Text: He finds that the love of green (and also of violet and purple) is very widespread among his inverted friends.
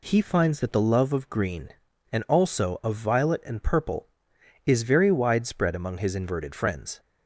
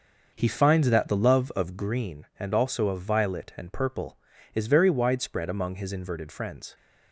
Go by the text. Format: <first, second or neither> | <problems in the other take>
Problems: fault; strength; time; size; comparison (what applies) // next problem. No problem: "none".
first | starts louder than the rest; noticeable; until 2.0 s; 6 dB